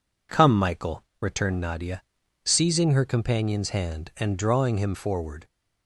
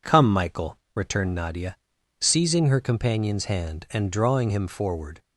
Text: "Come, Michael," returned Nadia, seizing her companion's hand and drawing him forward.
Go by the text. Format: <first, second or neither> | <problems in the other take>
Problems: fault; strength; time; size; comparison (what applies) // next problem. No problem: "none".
neither | none